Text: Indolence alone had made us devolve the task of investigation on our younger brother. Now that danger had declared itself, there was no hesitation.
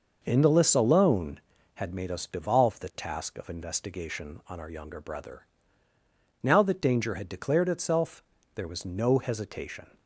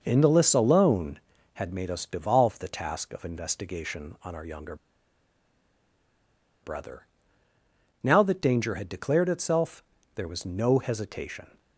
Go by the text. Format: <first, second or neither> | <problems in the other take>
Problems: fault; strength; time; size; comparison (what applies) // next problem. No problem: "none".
first | pauses between "younger" and "brother"; strong; at 4.7 s; 1.8 s long